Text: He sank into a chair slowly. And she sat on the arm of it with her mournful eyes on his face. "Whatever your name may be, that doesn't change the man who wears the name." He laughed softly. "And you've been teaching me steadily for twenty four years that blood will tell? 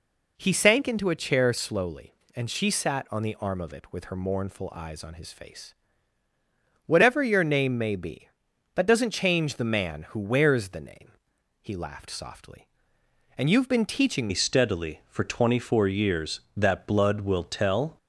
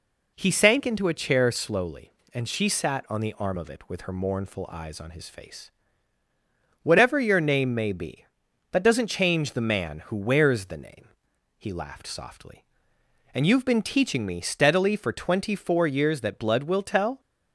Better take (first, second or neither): second